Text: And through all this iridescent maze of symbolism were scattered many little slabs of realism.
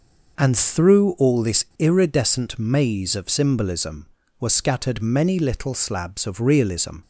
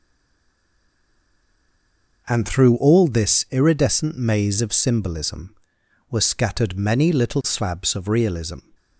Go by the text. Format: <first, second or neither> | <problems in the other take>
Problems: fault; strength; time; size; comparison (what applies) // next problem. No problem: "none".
first | stays silent before the first word; until 2.2 s; 2.2 s long